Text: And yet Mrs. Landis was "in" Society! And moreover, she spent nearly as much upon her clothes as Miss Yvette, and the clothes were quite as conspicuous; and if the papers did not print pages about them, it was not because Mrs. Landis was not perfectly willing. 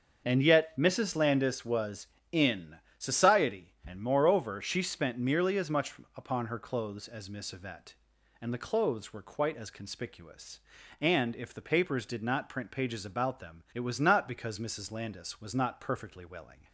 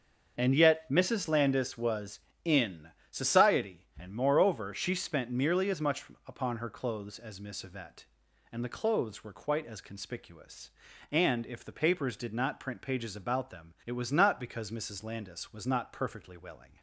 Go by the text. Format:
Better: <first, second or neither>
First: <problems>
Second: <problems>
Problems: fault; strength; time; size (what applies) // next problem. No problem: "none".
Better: neither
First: starts louder than the rest; until 1.2 s; 6.5 dB // pauses between "in" and "Society"; slight; at 2.7 s; 0.22 s long // pauses between "much" and "upon"; slight; at 5.9 s; 0.24 s long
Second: starts louder than the rest; until 1.4 s; 6.5 dB // pauses between "in" and "Society"; slight; at 2.8 s; 0.22 s long // pauses between "much" and "upon"; slight; at 6.0 s; 0.24 s long